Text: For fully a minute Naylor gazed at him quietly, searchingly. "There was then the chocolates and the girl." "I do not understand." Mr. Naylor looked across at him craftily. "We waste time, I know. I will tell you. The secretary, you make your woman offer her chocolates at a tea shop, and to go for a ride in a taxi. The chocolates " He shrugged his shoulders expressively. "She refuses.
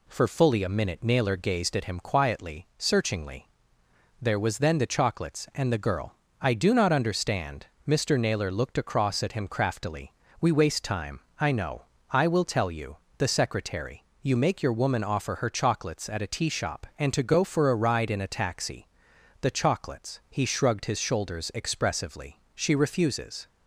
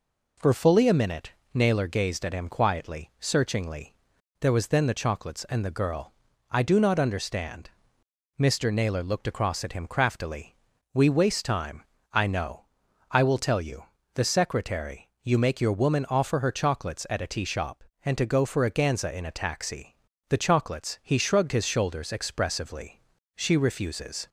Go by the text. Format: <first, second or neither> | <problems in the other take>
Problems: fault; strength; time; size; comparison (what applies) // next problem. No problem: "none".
first | pauses between "minute" and "Naylor"; slight; at 1.3 s; 0.20 s long // says "ganza" for "ride"; at 18.7 s